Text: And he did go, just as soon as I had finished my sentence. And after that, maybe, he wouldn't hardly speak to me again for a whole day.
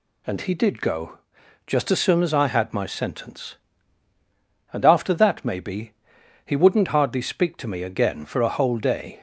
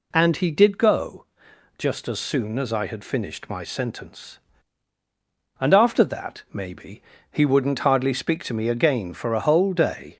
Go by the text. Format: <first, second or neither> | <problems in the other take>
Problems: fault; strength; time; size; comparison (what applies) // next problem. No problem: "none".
second | skips "finished"; at 2.7 s